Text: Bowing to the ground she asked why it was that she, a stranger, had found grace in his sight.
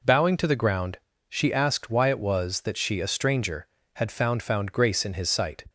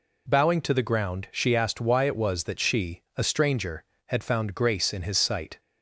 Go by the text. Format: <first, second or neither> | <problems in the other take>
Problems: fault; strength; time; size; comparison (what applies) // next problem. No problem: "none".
second | pauses between "ground" and "she"; slight; at 0.9 s; 0.30 s long // says "found" twice; at 4.4 s